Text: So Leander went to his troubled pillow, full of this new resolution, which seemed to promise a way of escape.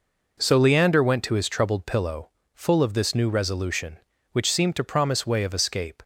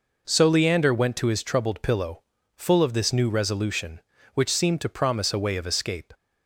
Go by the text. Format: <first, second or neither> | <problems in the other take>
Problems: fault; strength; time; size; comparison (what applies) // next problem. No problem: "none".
second | skips "a"; at 5.2 s